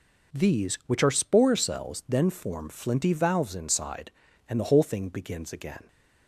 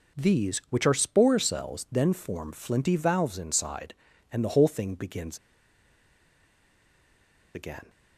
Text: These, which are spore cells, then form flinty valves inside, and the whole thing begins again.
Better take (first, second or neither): first